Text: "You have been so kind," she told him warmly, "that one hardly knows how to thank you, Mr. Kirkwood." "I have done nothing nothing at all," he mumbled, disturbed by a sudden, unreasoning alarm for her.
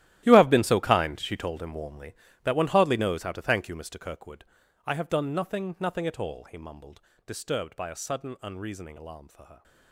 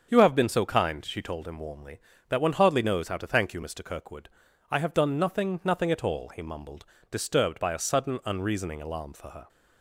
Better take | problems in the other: second | gets quieter; strong; throughout; 16.5 dB // starts louder than the rest; strong; until 1.2 s; 14 dB; also in the second

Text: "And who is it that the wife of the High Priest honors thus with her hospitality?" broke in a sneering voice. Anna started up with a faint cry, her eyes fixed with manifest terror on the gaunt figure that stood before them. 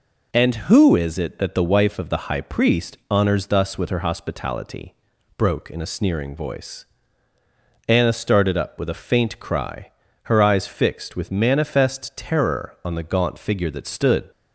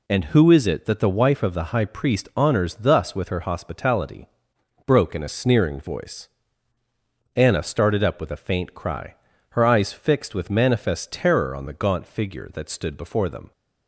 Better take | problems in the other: second | stops before "before them"; at 14.3 s

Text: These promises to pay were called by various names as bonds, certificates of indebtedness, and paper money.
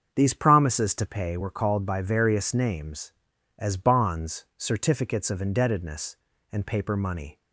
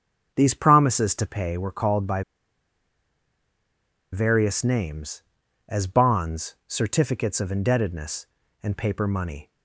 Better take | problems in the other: first | starts louder than the rest; until 1.3 s; 7 dB; also in the first // pauses between "by" and "various"; strong; at 2.2 s; 1.8 s long

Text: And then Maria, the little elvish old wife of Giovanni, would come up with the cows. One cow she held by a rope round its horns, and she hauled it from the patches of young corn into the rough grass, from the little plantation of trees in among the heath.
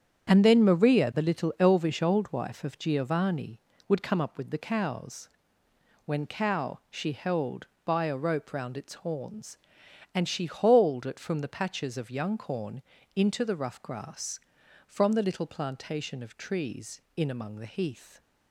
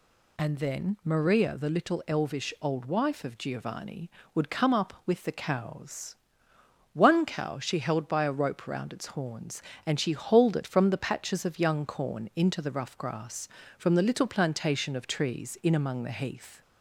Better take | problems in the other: second | starts louder than the rest; strong; until 1.3 s; 8 dB // says "When" for "One"; at 6.0 s // pauses between "corn" and "into"; slight; at 12.8 s; 0.32 s long

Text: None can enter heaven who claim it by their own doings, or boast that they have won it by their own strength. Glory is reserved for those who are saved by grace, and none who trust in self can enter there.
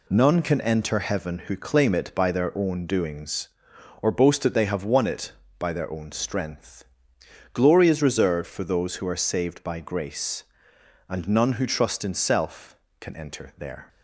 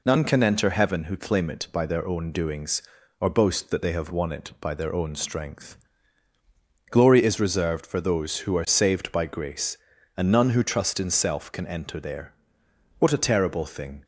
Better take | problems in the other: first | goes on to say "What a terrible thing"; noticeable; from 12.9 s on; 1.0 s long

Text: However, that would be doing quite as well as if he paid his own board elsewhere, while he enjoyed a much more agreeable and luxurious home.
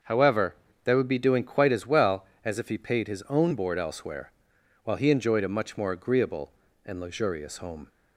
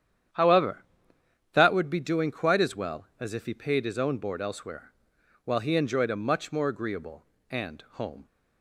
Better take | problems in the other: first | starts louder than the rest; strong; until 2.0 s; 9.5 dB; also in the first // skips "luxurious"; at 7.8 s

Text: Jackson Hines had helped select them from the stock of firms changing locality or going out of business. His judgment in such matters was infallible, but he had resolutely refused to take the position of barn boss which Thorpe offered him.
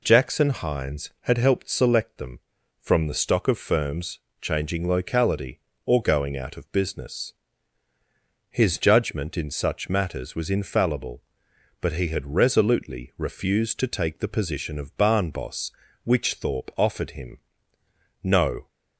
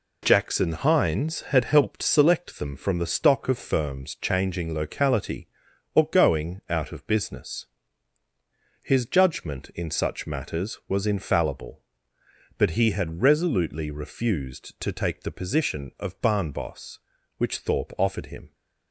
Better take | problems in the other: second | pauses between "firms" and "changing"; slight; at 4.1 s; 0.22 s long // goes on to say "No"; slight; from 18.2 s on; 0.46 s long

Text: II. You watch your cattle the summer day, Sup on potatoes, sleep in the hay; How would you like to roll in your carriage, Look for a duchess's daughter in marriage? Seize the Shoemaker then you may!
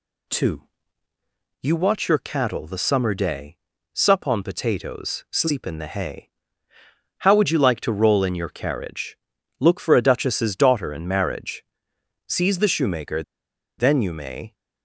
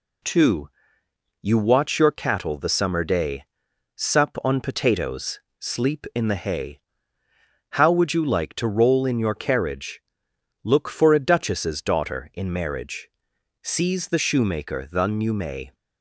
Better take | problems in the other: second | pauses between "Shoemaker" and "then"; noticeable; at 13.2 s; 0.56 s long

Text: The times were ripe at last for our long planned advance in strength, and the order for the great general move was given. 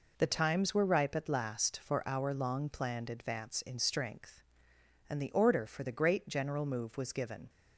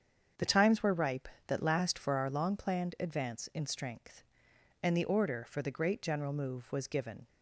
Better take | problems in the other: first | starts louder than the rest; strong; until 1.5 s; 7.5 dB // says "that" for "at"; at 1.4 s

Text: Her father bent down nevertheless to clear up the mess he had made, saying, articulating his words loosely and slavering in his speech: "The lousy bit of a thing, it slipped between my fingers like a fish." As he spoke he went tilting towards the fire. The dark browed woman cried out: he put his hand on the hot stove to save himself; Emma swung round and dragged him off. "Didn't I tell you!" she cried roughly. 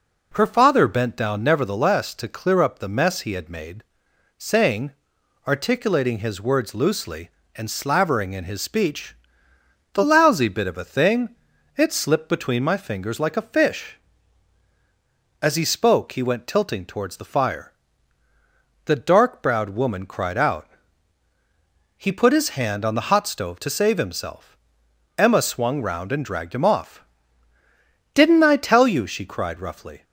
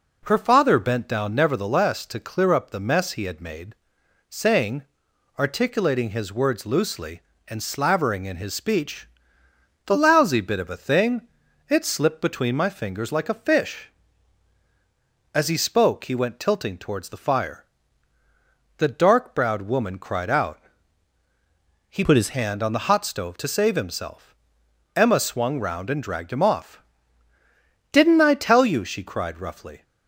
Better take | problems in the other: first | changes voice from "put" to "his"; from 22.0 to 22.3 s; 0.3 s long

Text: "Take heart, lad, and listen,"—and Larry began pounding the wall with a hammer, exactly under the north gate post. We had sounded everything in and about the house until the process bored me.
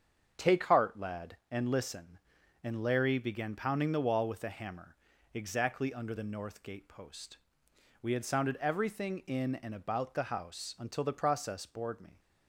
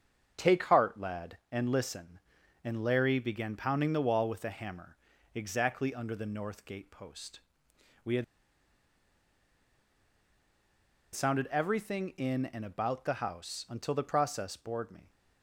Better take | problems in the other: first | starts louder than the rest; strong; until 1.3 s; 7.5 dB; strong in the first // pauses between "had" and "sounded"; strong; at 8.2 s; 2.9 s long

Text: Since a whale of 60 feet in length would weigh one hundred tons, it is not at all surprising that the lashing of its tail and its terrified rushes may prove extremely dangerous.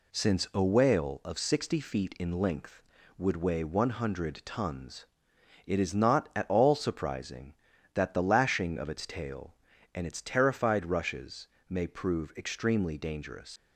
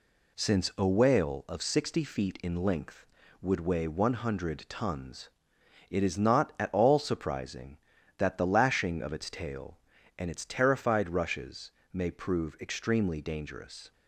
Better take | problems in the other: second | pauses between "rushes" and "may"; slight; at 11.4 s; 0.22 s long; slight in the second // leaves "dangerous" unfinished; at 13.5 s; 120 ms

